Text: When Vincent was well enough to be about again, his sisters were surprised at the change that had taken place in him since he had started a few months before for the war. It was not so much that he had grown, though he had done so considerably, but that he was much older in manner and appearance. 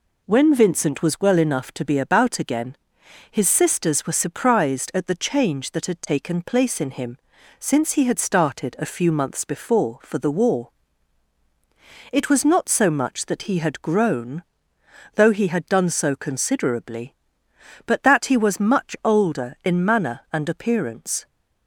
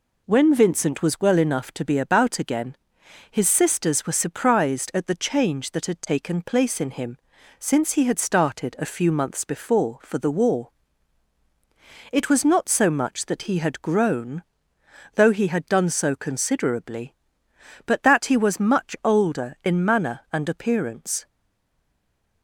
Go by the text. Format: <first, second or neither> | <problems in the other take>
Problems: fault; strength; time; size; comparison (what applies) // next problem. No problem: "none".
first | pauses between "him" and "since"; at 7.1 s; 0.42 s long; also in the first // stays silent after the last word; noticeable; from 21.2 s on; 1.2 s long